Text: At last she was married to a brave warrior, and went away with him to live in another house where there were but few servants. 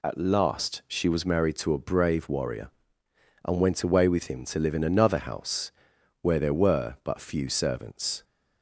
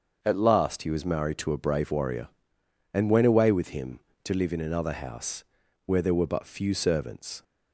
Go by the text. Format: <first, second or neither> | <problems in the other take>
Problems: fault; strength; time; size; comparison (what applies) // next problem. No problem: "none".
first | starts louder than the rest; until 1.2 s; 6.5 dB // says "he" for "she"; at 0.8 s // pauses between "house" and "where"; at 5.4 s; 0.40 s long; noticeable in the first